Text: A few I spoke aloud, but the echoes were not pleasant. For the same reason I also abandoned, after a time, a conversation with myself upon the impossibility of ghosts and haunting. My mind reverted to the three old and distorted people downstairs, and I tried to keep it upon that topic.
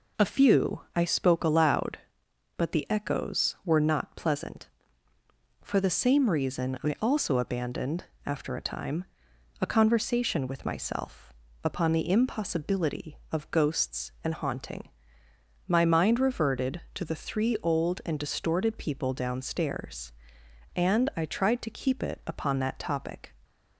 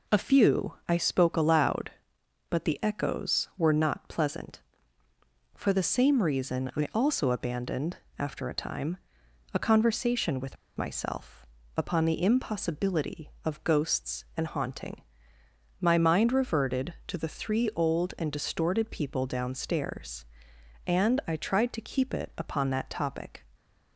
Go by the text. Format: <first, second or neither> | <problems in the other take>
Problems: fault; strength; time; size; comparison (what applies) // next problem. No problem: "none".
first | pauses between "with" and "myself"; slight; at 10.5 s; 0.21 s long // pauses between "myself" and "upon"; slight; at 11.4 s; 0.32 s long; slight in the first